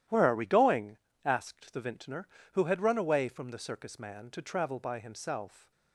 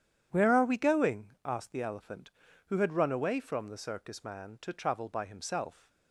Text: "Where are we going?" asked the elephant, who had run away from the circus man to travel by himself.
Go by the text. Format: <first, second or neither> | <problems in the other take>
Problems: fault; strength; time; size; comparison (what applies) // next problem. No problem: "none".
second | starts louder than the rest; strong; until 1.3 s; 12 dB; strong in the second // says "vintner" for "elephant"; at 1.8 s